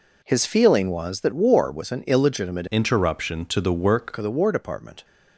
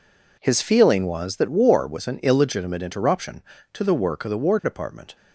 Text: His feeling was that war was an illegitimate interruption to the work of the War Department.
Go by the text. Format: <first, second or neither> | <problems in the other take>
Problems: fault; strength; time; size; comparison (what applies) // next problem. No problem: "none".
second | changes voice from "interruption" to "work"; from 2.7 to 4.1 s; 1.4 s long